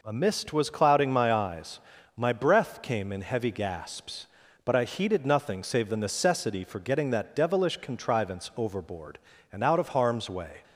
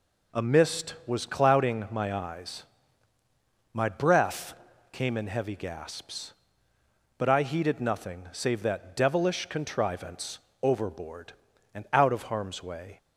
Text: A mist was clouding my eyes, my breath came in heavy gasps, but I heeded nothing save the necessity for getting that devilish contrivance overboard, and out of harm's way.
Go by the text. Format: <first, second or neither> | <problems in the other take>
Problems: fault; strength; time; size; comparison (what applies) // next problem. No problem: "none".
first | pauses between "breath" and "came"; at 4.5 s; 0.38 s long // skips "the necessity for getting"; at 8.6 s // pauses between "contrivance" and "overboard"; slight; at 10.3 s; 0.24 s long